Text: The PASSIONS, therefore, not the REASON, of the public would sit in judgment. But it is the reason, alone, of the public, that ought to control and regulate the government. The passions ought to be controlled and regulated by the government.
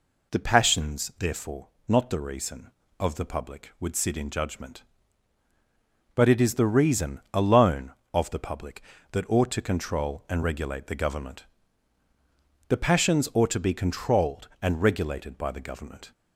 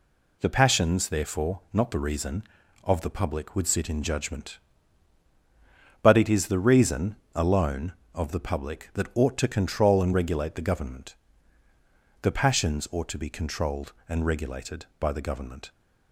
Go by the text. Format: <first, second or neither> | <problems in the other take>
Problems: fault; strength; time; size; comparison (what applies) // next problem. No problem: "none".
neither | none